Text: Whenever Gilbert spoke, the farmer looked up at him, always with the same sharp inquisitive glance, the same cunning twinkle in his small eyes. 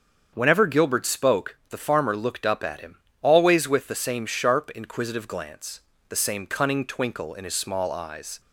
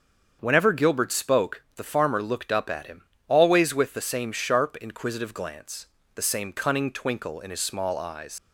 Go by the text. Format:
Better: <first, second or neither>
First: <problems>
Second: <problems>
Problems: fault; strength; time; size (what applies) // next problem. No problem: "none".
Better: first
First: starts louder than the rest; strong; until 1.3 s; 7.5 dB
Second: starts louder than the rest; until 1.4 s; 7 dB // leaves "eyes" unfinished; at 8.3 s; 80 ms